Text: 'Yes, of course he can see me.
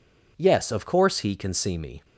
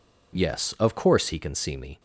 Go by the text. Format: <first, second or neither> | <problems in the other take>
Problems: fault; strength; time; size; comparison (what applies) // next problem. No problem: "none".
neither | none